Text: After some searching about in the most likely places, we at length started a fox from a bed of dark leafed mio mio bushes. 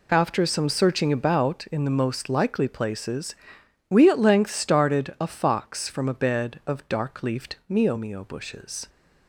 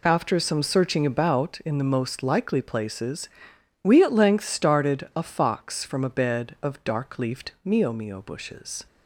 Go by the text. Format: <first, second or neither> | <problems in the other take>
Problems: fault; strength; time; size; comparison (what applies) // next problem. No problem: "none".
neither | none